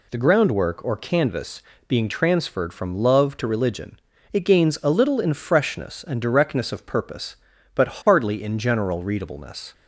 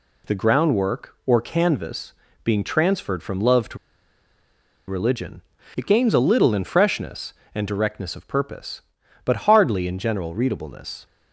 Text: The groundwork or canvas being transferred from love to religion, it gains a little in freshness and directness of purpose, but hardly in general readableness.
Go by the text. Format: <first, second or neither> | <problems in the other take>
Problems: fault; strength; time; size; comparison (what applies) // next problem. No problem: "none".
first | pauses between "canvas" and "being"; slight; at 2.1 s; 0.30 s long; slight in the first // pauses between "to" and "religion"; at 3.7 s; 1.1 s long